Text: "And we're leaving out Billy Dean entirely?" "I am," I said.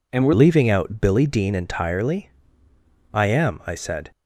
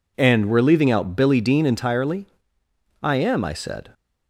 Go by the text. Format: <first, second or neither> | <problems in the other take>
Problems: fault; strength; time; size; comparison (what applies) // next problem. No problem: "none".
second | changes voice at "leaving"; from 0.3 s on; 3.8 s long